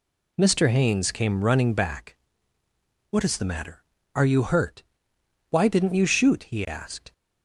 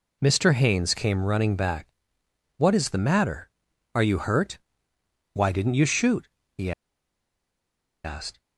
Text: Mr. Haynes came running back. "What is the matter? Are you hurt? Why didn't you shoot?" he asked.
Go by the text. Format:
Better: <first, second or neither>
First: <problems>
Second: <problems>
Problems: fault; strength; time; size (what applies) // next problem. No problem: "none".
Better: first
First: none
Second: pauses between "he" and "asked"; strong; at 6.7 s; 1.3 s long